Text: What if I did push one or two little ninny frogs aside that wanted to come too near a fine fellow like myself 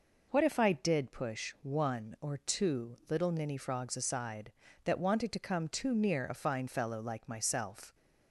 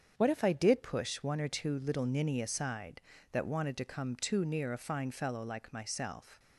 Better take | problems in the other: first | starts louder than the rest; strong; until 1.2 s; 7.5 dB // skips "frogs"; at 2.4 s

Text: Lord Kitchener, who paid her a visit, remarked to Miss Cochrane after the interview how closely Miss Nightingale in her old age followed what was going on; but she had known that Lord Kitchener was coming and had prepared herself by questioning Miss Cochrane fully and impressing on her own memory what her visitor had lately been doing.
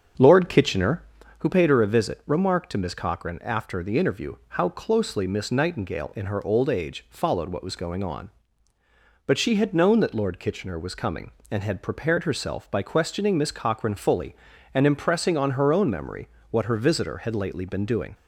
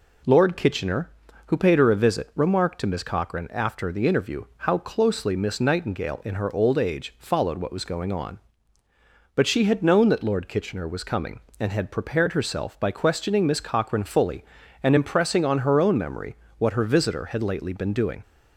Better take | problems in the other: second | starts louder than the rest; strong; until 1.4 s; 7 dB // pauses between "memory" and "what"; slight; at 16.2 s; 0.24 s long; slight in the second

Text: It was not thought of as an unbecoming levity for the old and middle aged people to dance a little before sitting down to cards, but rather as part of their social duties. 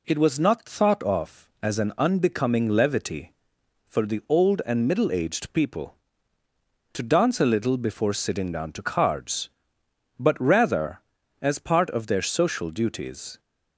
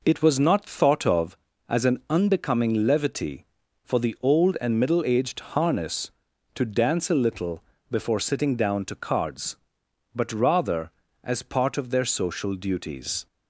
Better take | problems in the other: first | says "harness" for "people"; at 5.5 s // pauses between "little" and "before"; slight; at 7.6 s; 0.26 s long

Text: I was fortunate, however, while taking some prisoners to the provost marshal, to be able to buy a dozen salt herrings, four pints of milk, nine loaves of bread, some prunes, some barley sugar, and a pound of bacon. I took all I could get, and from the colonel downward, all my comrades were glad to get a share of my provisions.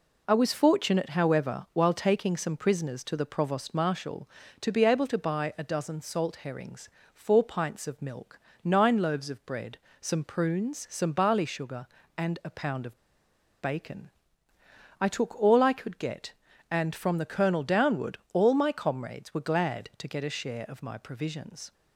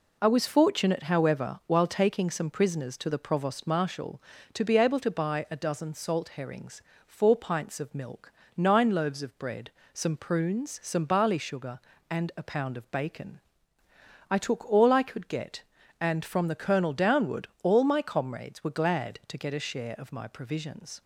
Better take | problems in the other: second | pauses between "of" and "bacon"; noticeable; at 12.9 s; 0.62 s long

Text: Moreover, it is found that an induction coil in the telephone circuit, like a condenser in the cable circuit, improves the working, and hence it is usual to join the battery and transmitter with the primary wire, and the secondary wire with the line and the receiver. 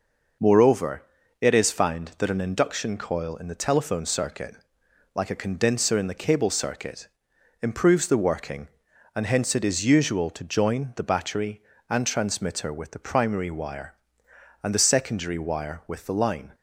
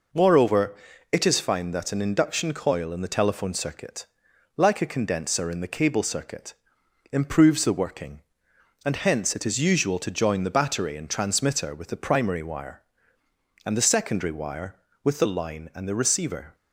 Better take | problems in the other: second | stops before "and the receiver"; at 16.5 s

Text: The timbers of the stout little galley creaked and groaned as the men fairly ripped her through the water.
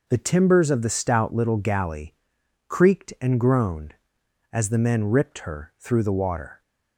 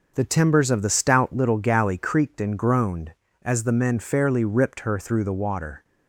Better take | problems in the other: second | pauses between "galley" and "creaked"; noticeable; at 2.1 s; 0.54 s long // skips "fairly"; at 5.0 s

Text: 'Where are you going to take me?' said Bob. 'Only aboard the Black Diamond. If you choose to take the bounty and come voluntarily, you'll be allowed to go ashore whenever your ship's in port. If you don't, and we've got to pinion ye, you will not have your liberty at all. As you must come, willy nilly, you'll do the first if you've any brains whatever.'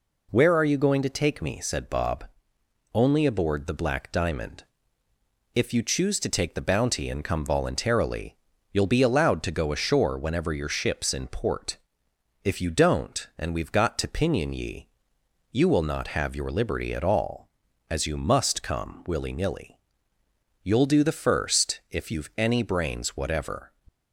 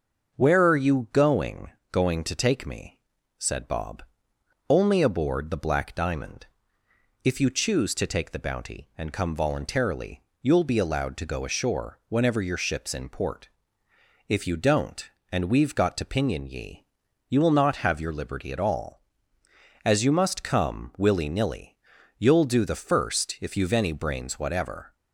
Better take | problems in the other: first | starts louder than the rest; until 1.3 s; 6.5 dB // says "going" twice; at 1.9 s

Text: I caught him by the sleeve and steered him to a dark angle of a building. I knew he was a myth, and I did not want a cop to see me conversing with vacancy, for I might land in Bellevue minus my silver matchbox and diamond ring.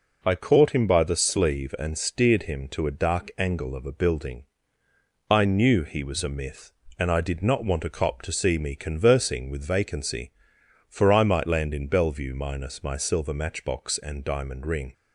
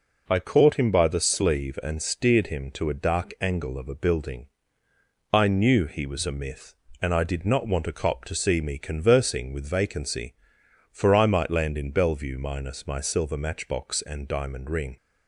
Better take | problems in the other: neither | none

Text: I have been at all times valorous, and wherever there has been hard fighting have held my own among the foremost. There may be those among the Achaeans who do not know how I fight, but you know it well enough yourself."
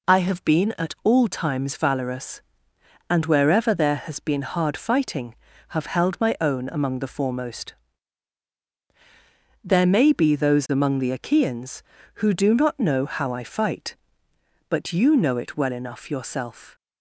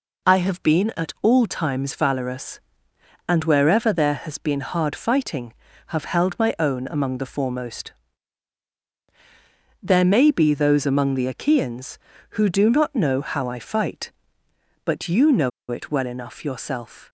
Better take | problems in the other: first | pauses between "know" and "it"; slight; at 15.5 s; 0.20 s long

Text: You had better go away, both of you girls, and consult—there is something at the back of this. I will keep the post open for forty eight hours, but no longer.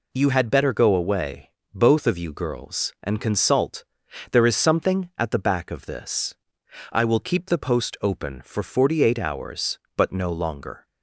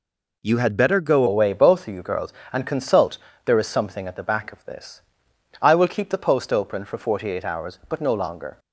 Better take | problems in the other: first | changes voice at "away"; from 1.2 s on; 7.3 s long

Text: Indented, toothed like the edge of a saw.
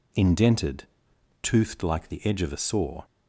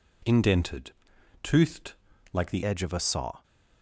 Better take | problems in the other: first | pauses between "toothed" and "like"; slight; at 1.9 s; 0.36 s long // changes voice at "edge"; from 2.6 s on; 0.8 s long

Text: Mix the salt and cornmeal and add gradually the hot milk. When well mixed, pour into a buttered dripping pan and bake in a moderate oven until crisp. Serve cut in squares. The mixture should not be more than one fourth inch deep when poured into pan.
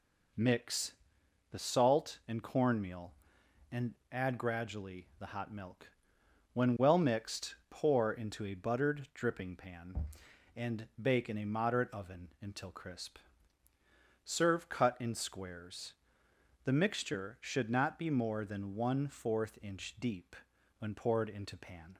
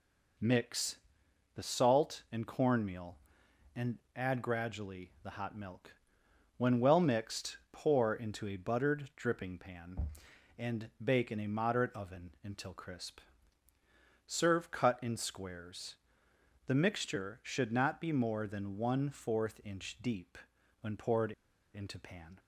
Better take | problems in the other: first | pauses between "Mix" and "the"; noticeable; at 0.9 s; 0.58 s long; noticeable in the first // pauses between "and" and "add"; slight; at 3.9 s; 0.18 s long; slight in the first // pauses between "deep" and "when"; at 20.3 s; 0.44 s long; also in the first // pauses between "poured" and "into"; at 21.3 s; 0.42 s long

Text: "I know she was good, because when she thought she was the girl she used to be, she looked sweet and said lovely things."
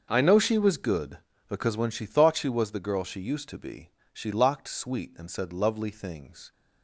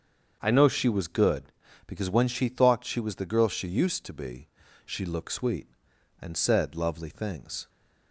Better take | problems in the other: second | starts louder than the rest; until 1.0 s; 6.5 dB; also in the second // says "locked" for "looked"; at 4.3 s

